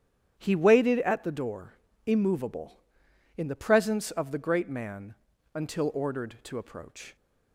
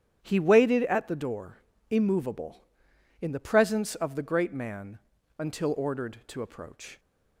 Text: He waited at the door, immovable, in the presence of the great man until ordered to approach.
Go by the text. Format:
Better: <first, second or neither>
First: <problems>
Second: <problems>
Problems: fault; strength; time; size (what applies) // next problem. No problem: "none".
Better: neither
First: starts louder than the rest; strong; until 1.3 s; 9.5 dB // pauses between "man" and "until"; at 5.1 s; 0.40 s long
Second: starts louder than the rest; strong; until 1.2 s; 9.5 dB // pauses between "man" and "until"; at 4.9 s; 0.40 s long